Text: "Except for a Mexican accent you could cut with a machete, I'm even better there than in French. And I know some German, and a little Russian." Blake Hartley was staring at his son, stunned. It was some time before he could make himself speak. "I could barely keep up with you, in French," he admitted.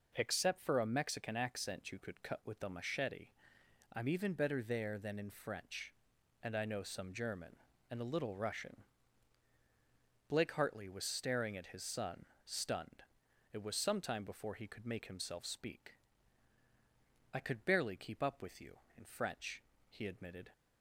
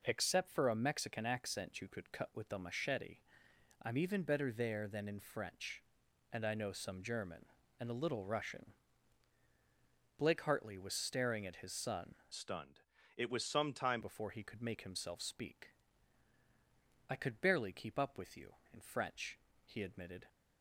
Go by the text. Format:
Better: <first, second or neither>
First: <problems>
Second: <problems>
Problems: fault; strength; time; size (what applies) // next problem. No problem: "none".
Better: first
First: none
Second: changes voice from "stunned" to "time"; from 12.3 to 13.9 s; 1.6 s long